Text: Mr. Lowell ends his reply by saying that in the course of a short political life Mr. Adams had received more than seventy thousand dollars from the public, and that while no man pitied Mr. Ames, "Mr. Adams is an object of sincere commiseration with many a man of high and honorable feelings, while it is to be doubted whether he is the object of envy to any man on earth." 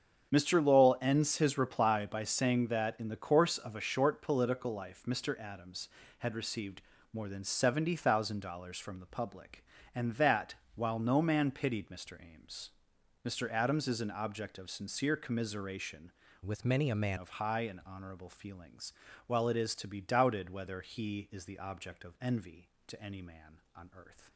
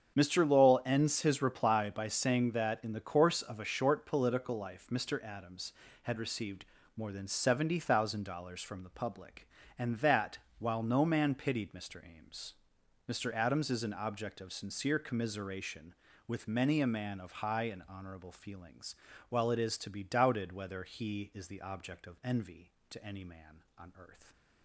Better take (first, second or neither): second